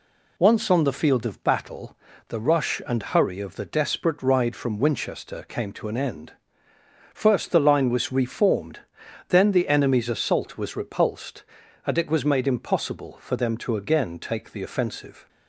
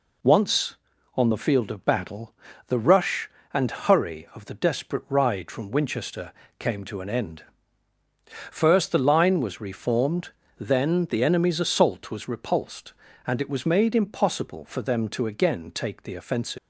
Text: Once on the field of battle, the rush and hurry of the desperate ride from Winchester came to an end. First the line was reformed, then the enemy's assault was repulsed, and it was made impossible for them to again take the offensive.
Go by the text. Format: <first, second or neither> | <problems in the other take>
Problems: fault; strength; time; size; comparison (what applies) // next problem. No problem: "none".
first | pauses between "Winchester" and "came"; slight; at 6.3 s; 0.26 s long // leaves "offensive" unfinished; at 16.5 s; 295 ms